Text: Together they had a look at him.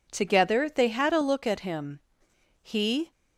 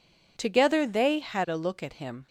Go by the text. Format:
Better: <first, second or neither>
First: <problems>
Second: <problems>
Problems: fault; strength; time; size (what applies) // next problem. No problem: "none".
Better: second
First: goes on to say "He"; slight; from 2.6 s on; 0.48 s long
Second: none